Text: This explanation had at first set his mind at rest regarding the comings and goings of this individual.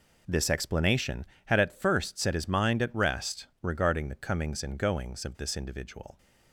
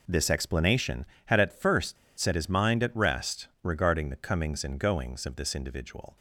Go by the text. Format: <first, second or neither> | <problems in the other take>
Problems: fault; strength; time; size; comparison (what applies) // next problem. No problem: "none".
first | pauses between "first" and "set"; slight; at 1.9 s; 0.23 s long